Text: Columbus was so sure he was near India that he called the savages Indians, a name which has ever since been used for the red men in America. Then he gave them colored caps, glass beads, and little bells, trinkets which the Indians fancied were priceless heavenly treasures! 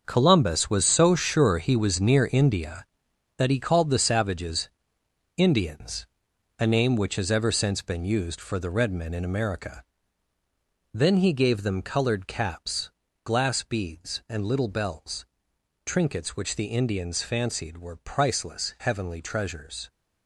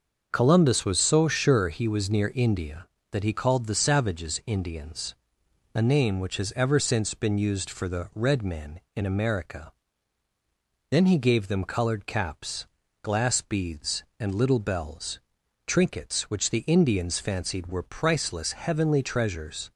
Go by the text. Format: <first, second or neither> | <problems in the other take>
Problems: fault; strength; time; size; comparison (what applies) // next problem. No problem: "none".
second | gets quieter; strong; throughout; 11 dB // starts louder than the rest; until 1.0 s; 6.5 dB; also in the second // pauses between "savages" and "Indians"; noticeable; at 4.6 s; 0.66 s long